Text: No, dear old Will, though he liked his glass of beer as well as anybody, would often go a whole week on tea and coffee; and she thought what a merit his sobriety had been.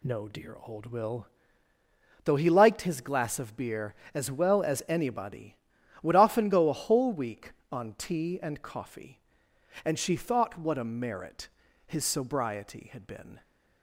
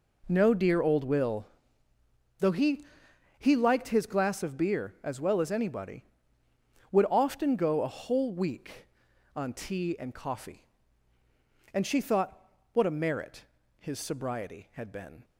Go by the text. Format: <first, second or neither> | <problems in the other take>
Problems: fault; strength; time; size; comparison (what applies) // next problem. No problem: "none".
first | says "he" twice; at 3.3 s // pauses between "thought" and "what"; slight; at 12.3 s; 0.34 s long // pauses between "merit" and "his"; slight; at 13.4 s; 0.34 s long; slight in the first